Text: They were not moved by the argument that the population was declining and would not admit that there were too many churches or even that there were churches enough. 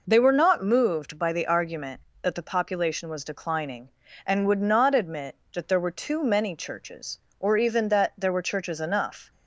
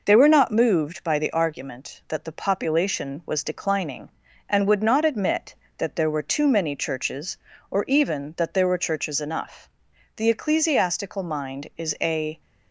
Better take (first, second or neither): first